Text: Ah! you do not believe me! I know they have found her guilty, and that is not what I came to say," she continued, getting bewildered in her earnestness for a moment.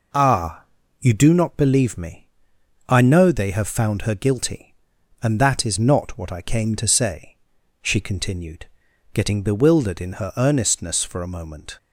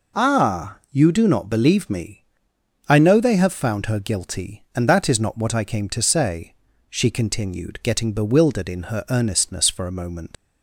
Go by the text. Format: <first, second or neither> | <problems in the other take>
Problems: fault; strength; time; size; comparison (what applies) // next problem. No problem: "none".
first | leaves "moment" unfinished; at 10.3 s; 70 ms